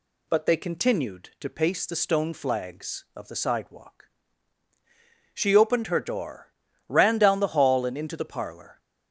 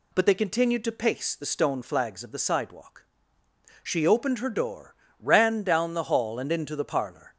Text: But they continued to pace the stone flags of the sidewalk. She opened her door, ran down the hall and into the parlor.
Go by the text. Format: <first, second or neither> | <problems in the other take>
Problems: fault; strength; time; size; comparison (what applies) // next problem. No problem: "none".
neither | none